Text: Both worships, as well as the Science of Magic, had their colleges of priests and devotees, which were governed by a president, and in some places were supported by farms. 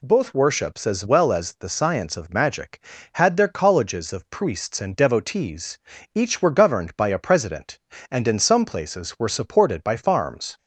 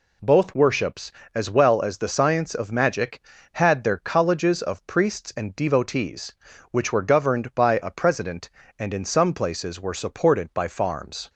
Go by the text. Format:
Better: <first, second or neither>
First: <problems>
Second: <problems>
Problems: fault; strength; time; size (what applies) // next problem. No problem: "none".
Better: second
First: says "each" for "which"; at 6.1 s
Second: none